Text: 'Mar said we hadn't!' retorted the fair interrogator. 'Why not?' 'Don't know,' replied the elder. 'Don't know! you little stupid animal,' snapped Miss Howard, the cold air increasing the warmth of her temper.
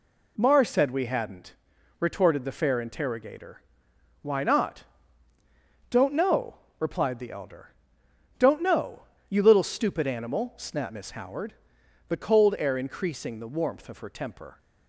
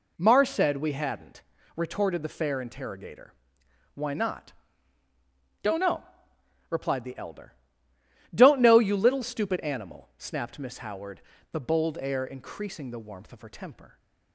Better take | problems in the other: first | says "bold" for "cold"; at 11.5 s

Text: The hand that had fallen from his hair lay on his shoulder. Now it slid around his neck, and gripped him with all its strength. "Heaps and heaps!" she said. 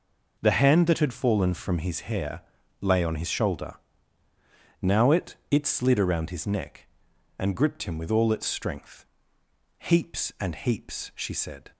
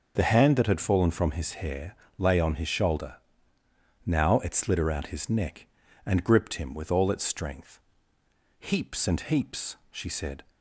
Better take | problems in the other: second | pauses between "hair" and "lay"; at 2.4 s; 0.38 s long; slight in the second // says "it" twice; at 5.4 s

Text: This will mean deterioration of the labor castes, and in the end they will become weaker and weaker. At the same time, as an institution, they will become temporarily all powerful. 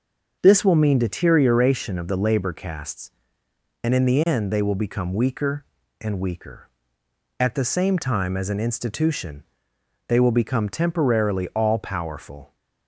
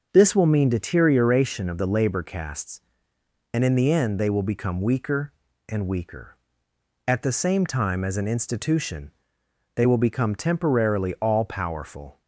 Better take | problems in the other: neither | starts louder than the rest; the same in both

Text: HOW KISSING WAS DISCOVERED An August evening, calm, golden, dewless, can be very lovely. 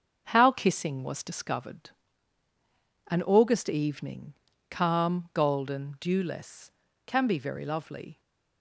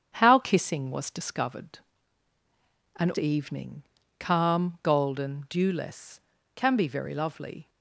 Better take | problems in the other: first | starts louder than the rest; strong; until 1.1 s; 7.5 dB; also in the first // pauses between "DISCOVERED" and "An"; at 1.7 s; 1.1 s long; also in the first // skips "August"; at 3.1 s

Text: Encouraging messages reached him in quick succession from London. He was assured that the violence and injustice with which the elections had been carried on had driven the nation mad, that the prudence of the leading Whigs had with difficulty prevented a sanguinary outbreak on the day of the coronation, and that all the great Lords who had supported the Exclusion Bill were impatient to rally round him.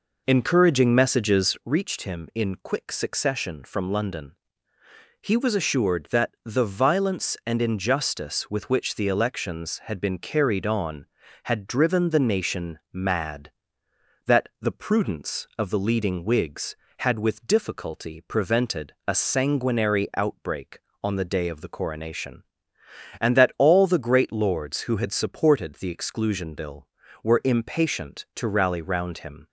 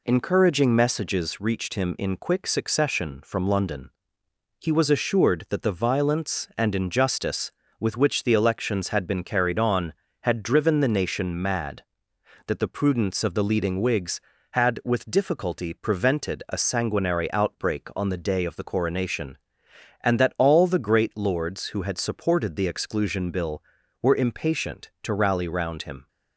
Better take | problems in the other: second | starts louder than the rest; noticeable; until 1.7 s; 4.5 dB

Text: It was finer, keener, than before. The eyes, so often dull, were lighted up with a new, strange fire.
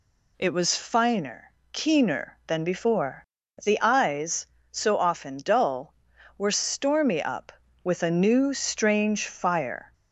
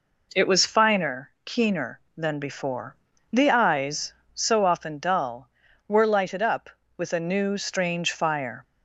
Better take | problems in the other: second | says "stormy" for "lighted"; at 6.5 s

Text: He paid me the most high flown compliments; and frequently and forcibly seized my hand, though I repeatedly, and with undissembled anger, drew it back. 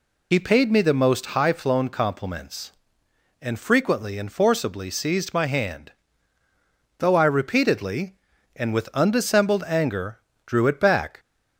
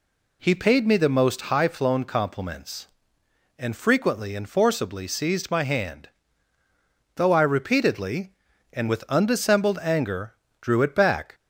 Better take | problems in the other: second | loses the start of "He"; at 0.3 s; 55 ms

